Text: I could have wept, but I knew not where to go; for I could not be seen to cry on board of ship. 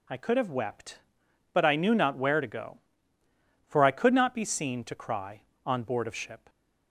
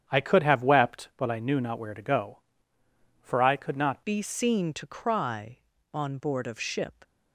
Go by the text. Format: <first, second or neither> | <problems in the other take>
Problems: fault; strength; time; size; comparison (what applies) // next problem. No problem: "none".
first | starts louder than the rest; strong; until 1.0 s; 9 dB // changes voice at "be"; from 4.0 s on; 3.0 s long